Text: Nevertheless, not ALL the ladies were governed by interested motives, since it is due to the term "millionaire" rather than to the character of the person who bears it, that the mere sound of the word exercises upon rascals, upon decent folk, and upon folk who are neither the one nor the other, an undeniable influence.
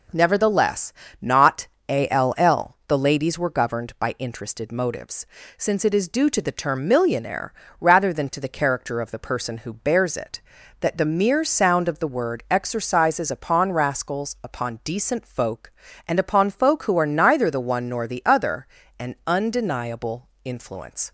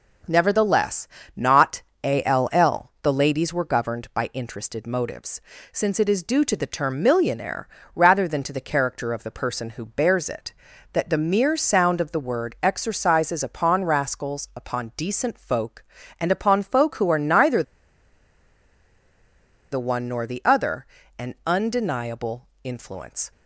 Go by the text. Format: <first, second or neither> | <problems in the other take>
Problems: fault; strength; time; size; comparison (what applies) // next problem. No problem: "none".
first | pauses between "not" and "ALL"; slight; at 1.8 s; 0.22 s long; slight in the first // pauses between "millionaire" and "rather"; slight; at 7.6 s; 0.28 s long; slight in the first // pauses between "neither" and "the"; strong; at 17.6 s; 2.1 s long // pauses between "undeniable" and "influence"; slight; at 22.4 s; 0.16 s long; slight in the first